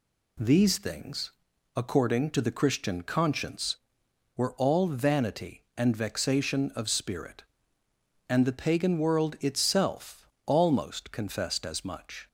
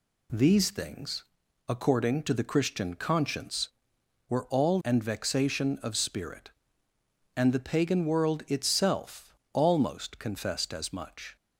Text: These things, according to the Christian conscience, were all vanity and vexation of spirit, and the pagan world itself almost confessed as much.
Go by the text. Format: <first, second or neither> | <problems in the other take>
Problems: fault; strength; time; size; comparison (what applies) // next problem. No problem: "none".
first | skips "vanity"; at 4.8 s // pauses between "itself" and "almost"; slight; at 9.3 s; 0.18 s long; slight in the first